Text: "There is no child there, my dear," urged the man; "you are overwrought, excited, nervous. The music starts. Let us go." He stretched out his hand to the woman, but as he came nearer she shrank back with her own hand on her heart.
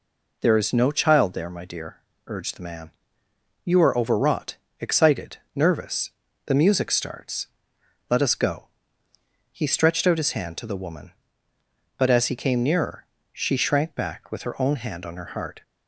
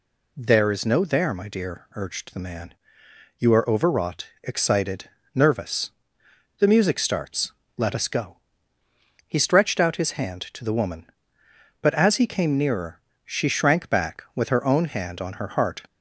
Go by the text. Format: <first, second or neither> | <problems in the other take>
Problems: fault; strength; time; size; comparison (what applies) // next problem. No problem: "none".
first | skips "child"; at 1.0 s // pauses between "nearer" and "she"; slight; at 13.0 s; 0.24 s long; slight in the first